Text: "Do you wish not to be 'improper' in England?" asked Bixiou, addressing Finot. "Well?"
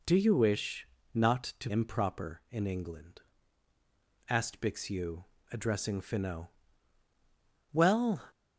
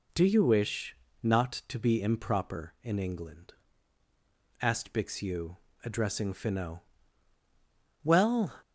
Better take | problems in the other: second | pauses between "wish" and "not"; slight; at 0.8 s; 0.26 s long; slight in the second // skips "be"; at 1.7 s

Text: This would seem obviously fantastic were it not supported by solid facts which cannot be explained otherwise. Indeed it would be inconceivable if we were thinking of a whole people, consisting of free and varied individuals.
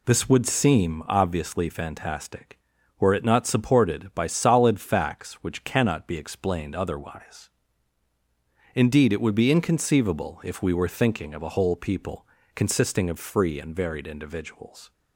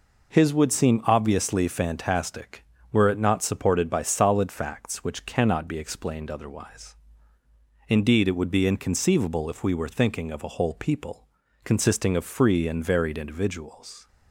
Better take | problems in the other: first | says "His" for "This"; at 0.3 s

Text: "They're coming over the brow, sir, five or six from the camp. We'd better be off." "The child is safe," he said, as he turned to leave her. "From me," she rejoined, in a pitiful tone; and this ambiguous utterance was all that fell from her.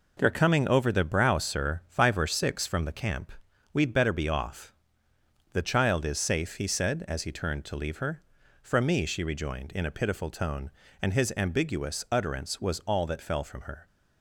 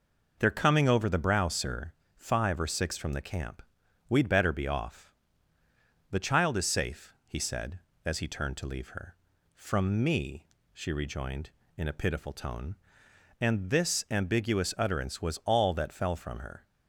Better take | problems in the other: second | says "his" for "this"; at 11.1 s

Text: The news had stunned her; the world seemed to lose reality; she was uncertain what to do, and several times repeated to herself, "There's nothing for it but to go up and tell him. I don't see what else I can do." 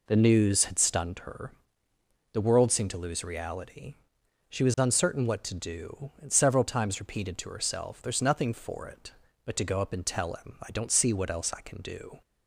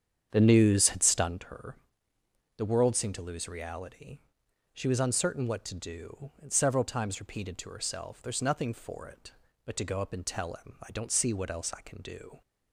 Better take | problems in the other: first | starts louder than the rest; strong; until 1.5 s; 8 dB

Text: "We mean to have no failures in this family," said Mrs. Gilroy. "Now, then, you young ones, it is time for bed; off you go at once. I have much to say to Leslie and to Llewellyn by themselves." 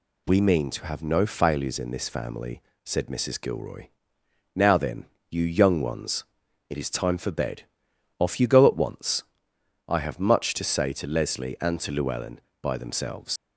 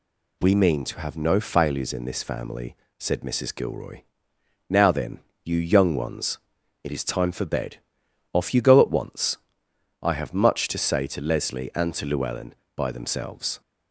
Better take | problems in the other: second | leaves "themselves" unfinished; at 13.3 s; 105 ms

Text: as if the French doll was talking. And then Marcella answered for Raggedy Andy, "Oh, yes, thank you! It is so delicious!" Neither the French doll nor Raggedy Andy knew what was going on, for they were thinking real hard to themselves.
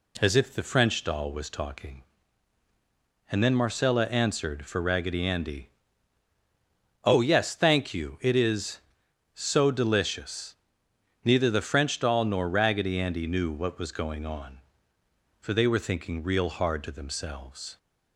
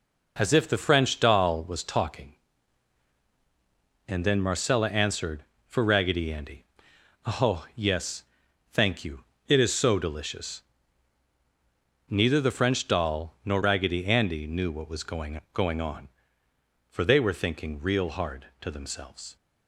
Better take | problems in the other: first | says "going" twice; at 15.5 s

